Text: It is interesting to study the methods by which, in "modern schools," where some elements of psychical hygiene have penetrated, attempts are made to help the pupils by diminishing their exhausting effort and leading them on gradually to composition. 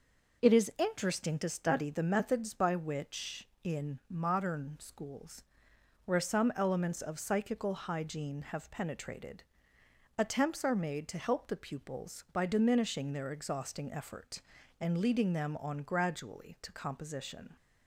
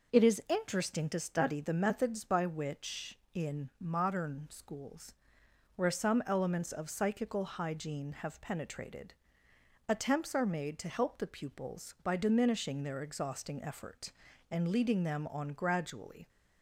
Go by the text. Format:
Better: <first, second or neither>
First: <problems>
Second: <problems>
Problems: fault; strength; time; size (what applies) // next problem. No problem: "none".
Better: first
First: none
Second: stops before "to composition"; at 16.2 s